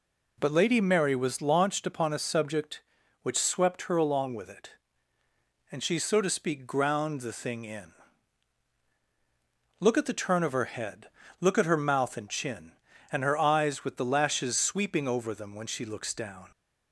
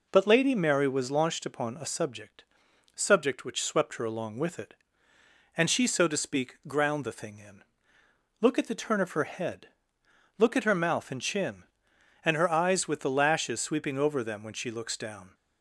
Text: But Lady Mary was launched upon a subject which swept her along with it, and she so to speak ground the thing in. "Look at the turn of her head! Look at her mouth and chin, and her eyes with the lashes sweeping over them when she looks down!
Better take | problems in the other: first | says "subject" twice; at 2.9 s

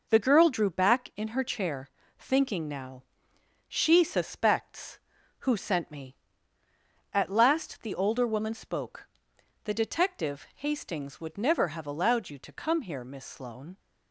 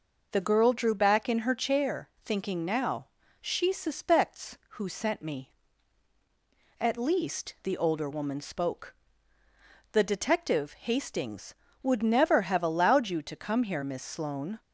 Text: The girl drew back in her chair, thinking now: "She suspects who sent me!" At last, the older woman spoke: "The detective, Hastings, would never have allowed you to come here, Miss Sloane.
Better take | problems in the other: first | says "least" for "last"; at 6.9 s

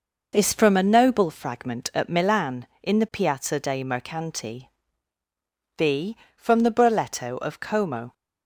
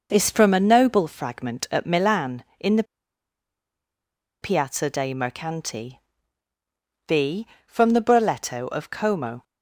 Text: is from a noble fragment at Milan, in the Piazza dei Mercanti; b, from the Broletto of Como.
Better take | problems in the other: first | pauses between "the" and "Piazza"; strong; at 2.8 s; 1.5 s long

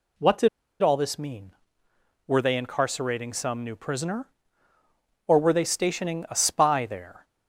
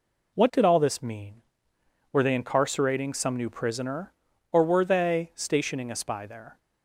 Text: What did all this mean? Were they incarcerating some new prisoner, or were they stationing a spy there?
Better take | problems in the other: second | pauses between "did" and "all"; slight; at 0.4 s; 0.33 s long

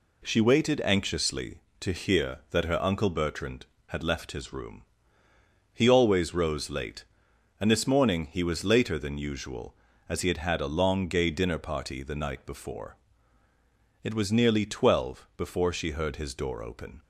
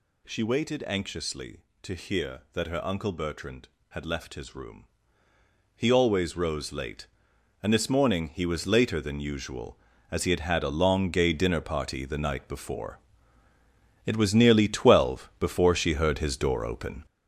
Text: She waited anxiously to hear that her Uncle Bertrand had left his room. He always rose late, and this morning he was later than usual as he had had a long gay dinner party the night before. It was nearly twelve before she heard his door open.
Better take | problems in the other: first | gets louder; throughout; 6.5 dB

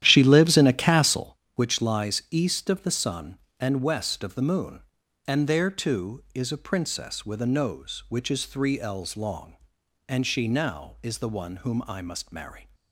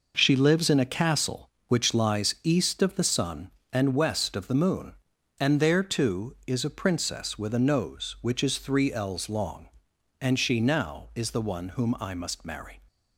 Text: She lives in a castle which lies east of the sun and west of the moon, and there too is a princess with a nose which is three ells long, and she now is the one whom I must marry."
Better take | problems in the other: second | starts louder than the rest; strong; until 1.4 s; 11.5 dB

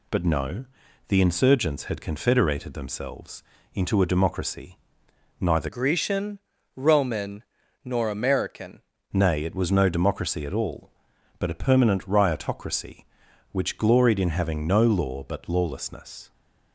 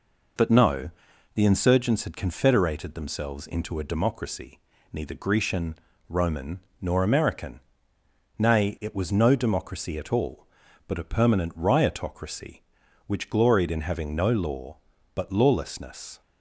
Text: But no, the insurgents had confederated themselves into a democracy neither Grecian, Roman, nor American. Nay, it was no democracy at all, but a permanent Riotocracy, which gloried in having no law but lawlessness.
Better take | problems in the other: second | pauses between "themselves" and "into"; slight; at 3.4 s; 0.30 s long // pauses between "democracy" and "neither"; noticeable; at 4.7 s; 0.62 s long; slight in the second // changes voice from "Grecian" to "American"; from 5.6 to 8.8 s; 3.2 s long

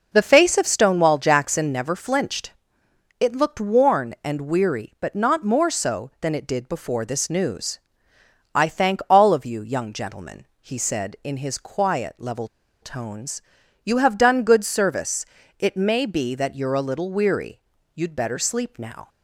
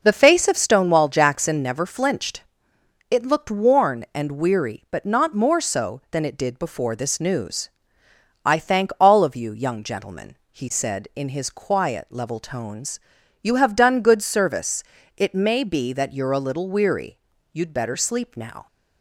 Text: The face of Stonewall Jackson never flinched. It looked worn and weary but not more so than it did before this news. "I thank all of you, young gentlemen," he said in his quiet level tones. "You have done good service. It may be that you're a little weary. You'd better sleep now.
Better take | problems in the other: second | pauses between "level" and "tones"; slight; at 12.4 s; 0.35 s long

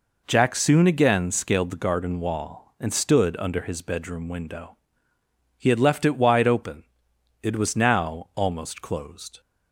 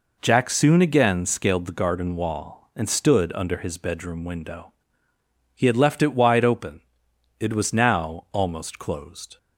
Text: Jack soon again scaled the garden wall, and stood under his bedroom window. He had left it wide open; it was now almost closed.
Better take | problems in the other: neither | none

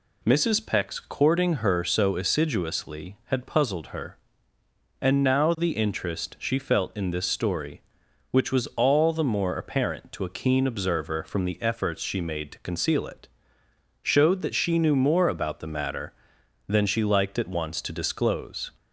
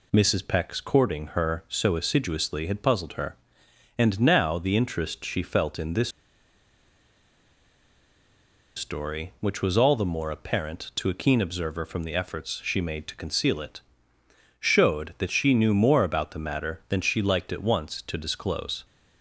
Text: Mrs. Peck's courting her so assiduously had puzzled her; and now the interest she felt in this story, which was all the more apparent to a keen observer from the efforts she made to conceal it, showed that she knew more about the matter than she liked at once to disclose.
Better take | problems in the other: first | pauses between "this" and "story"; strong; at 6.0 s; 2.6 s long

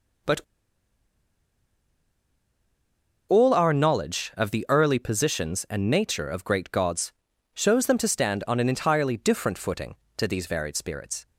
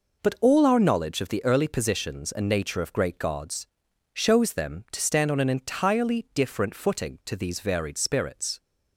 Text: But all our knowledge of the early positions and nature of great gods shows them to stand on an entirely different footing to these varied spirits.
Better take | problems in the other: second | pauses between "But" and "all"; strong; at 0.3 s; 2.9 s long // pauses between "gods" and "shows"; at 7.1 s; 0.40 s long; noticeable in the second

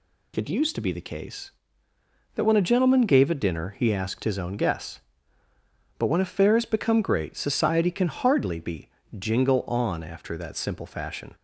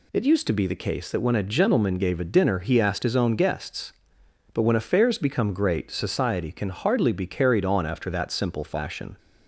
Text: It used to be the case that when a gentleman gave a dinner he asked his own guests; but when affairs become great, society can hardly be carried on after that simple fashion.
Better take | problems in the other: second | says "jingle" for "carried"; at 9.1 s

